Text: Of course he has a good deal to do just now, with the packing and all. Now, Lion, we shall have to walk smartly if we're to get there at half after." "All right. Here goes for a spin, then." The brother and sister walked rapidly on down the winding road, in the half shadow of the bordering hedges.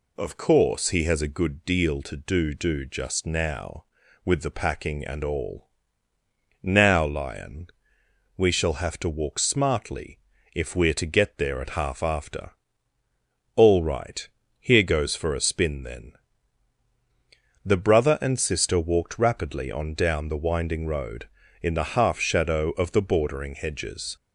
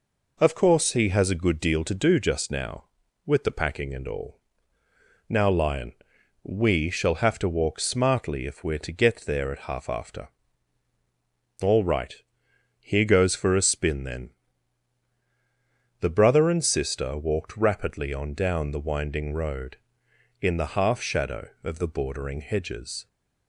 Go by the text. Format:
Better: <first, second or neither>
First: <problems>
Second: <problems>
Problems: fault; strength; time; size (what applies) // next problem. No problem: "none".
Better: second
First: says "do" twice; at 2.5 s // pauses between "smartly" and "if"; slight; at 10.1 s; 0.36 s long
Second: none